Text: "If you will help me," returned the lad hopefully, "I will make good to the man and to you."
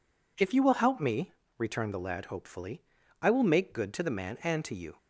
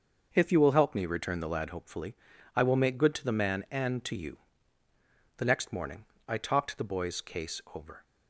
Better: first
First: none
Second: goes on to say "The next morning I talked the boy's case over"; strong; from 5.3 s on; 2.6 s long

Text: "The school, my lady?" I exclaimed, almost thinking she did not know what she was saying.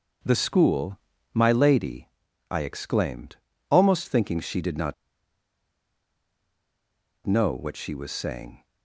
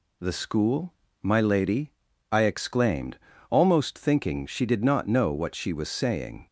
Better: second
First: starts louder than the rest; until 1.5 s; 6.5 dB // pauses between "not" and "know"; strong; at 4.9 s; 2.3 s long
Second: none

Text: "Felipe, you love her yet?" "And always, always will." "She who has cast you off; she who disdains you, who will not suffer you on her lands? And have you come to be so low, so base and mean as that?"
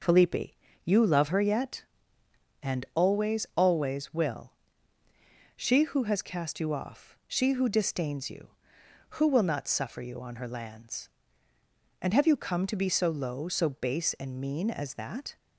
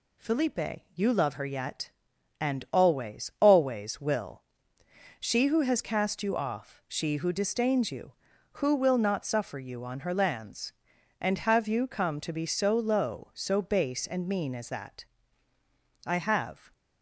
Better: first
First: none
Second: goes on to say "I have"; noticeable; from 16.0 s on; 0.68 s long

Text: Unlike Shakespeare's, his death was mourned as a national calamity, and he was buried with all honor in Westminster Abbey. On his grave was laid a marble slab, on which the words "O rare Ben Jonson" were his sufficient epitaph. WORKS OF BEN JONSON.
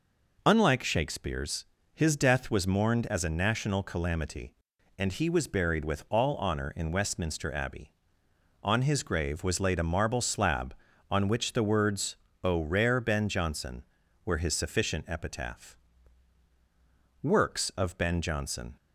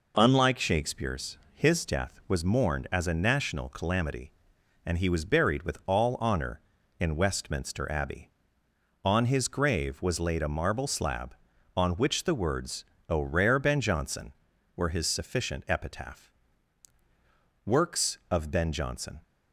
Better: neither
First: pauses between "words" and "O"; slight; at 12.1 s; 0.26 s long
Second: pauses between "words" and "O"; slight; at 12.8 s; 0.24 s long

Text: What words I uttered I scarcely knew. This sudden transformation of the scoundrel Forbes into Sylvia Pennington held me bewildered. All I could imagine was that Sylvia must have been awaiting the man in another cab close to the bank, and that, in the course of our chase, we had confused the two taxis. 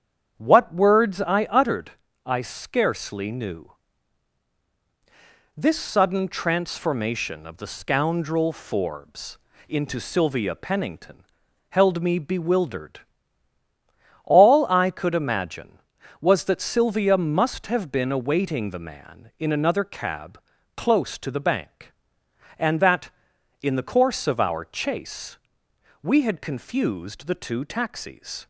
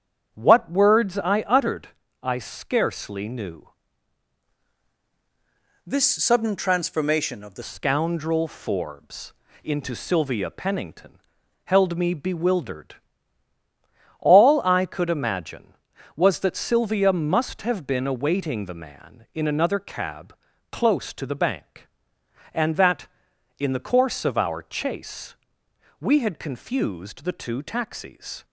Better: first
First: starts louder than the rest; strong; until 1.3 s; 8 dB // pauses between "uttered" and "I"; slight; at 1.9 s; 0.34 s long // pauses between "Forbes" and "into"; slight; at 9.3 s; 0.32 s long // pauses between "Pennington" and "held"; noticeable; at 11.2 s; 0.46 s long // pauses between "cab" and "close"; at 20.3 s; 0.38 s long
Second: starts louder than the rest; strong; until 1.3 s; 8 dB // pauses between "uttered" and "I"; slight; at 1.8 s; 0.34 s long // changes voice from "This" to "the"; from 5.8 to 7.6 s; 1.8 s long // pauses between "Forbes" and "into"; slight; at 9.3 s; 0.32 s long // pauses between "Pennington" and "held"; noticeable; at 11.1 s; 0.46 s long // pauses between "cab" and "close"; at 20.3 s; 0.38 s long

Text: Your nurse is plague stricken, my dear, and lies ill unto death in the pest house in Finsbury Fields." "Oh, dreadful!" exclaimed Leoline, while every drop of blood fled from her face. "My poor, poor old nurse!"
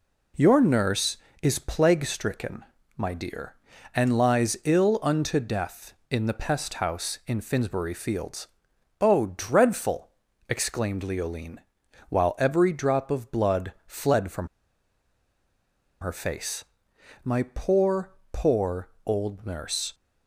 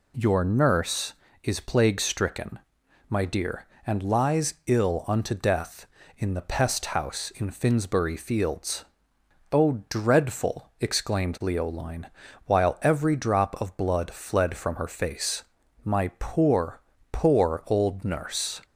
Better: second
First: pauses between "blood" and "fled"; slight; at 13.7 s; 0.16 s long // pauses between "from" and "her"; strong; at 14.4 s; 1.5 s long // pauses between "poor" and "old"; slight; at 18.9 s; 0.16 s long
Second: none

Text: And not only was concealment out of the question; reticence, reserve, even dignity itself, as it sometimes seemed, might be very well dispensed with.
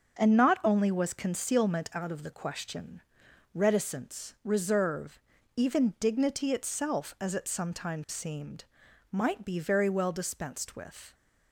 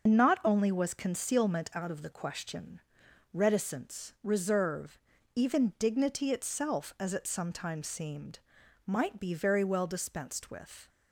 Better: first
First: starts louder than the rest; until 1.2 s; 6.5 dB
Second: loses the start of "And"; at 0.0 s; 85 ms // starts louder than the rest; noticeable; until 1.1 s; 6 dB

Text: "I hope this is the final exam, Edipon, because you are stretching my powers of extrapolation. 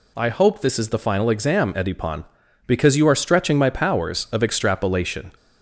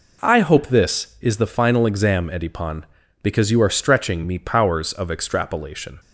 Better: first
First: none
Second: says "me" for "my"; at 4.2 s

